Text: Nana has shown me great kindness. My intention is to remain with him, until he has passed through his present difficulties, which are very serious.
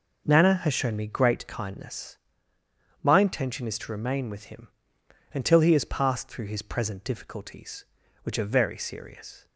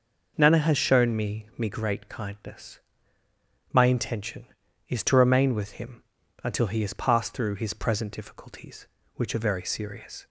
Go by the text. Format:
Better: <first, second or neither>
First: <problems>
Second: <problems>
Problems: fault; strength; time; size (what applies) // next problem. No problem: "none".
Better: first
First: none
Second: says "me" twice; at 1.5 s